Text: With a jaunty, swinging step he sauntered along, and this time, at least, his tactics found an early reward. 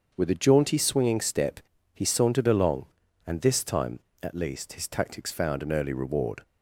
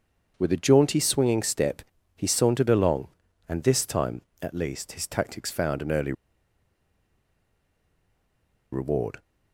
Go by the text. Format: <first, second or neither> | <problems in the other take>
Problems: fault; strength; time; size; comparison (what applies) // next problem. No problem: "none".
first | starts louder than the rest; until 1.3 s; 7 dB; also in the first // pauses between "step" and "he"; slight; at 1.8 s; 0.34 s long; slight in the first // pauses between "early" and "reward"; strong; at 6.1 s; 2.6 s long